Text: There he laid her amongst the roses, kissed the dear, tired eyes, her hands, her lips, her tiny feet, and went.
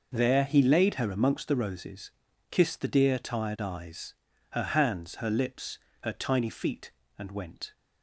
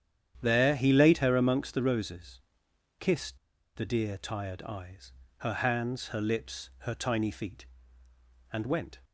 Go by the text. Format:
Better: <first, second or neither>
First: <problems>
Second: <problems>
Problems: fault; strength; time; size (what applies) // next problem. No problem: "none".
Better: first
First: none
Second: starts louder than the rest; strong; until 1.4 s; 9.5 dB // pauses between "kissed" and "the"; at 3.3 s; 0.38 s long